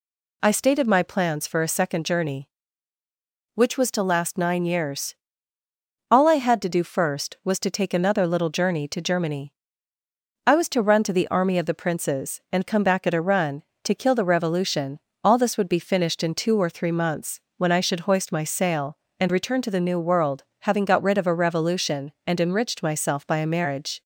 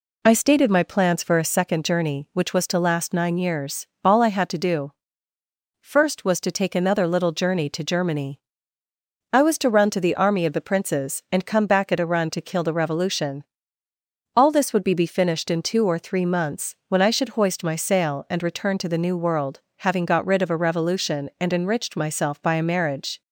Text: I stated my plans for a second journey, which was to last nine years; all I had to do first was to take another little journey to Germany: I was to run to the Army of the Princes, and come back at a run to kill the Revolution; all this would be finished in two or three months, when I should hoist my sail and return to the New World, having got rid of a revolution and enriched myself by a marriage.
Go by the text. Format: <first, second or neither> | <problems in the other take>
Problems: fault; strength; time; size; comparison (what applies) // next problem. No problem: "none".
first | pauses between "do" and "first"; noticeable; at 4.9 s; 0.88 s long // says "be" twice; at 14.9 s